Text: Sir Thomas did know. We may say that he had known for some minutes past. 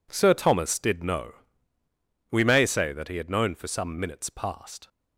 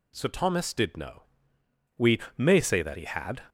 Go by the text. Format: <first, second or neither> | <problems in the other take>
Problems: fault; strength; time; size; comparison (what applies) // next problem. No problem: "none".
first | pauses between "We" and "may"; slight; at 2.1 s; 0.18 s long // stops before "known for some minutes past"; at 3.4 s